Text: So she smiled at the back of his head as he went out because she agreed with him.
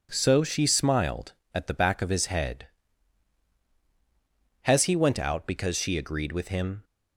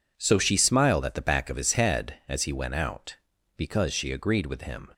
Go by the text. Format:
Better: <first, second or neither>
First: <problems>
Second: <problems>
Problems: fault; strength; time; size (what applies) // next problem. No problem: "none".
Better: second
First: says "has" for "as"; at 4.6 s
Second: none